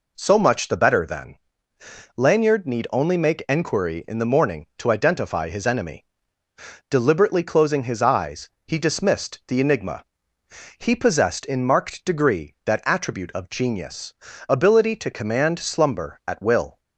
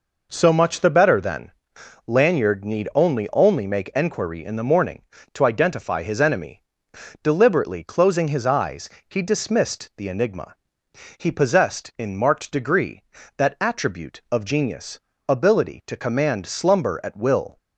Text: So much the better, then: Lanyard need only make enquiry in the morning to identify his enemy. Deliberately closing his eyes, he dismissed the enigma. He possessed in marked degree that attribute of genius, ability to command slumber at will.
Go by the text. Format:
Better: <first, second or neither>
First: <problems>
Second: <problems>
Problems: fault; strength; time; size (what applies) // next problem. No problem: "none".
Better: first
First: none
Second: says "only" twice; at 3.3 s